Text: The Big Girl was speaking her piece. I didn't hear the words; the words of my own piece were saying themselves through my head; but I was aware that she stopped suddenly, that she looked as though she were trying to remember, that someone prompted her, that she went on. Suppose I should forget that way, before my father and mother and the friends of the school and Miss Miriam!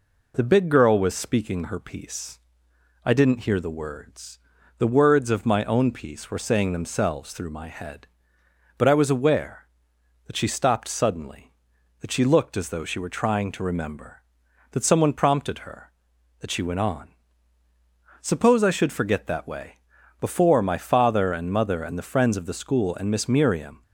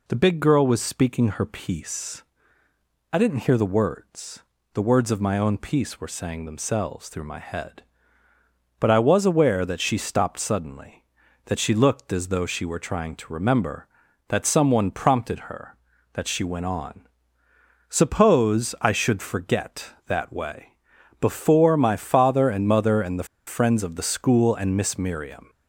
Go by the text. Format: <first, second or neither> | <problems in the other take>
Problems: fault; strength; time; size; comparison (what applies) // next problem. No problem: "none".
first | pauses between "the" and "friends"; slight; at 23.2 s; 0.22 s long